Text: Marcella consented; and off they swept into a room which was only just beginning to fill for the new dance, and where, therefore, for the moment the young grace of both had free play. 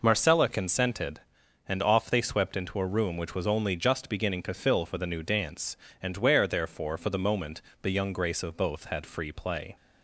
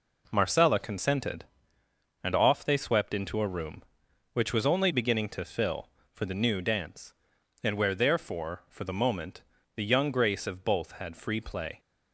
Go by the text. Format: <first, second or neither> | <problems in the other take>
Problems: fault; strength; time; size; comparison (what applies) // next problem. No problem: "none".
first | skips "just"; at 4.9 s // pauses between "moment" and "the"; slight; at 9.4 s; 0.34 s long; slight in the first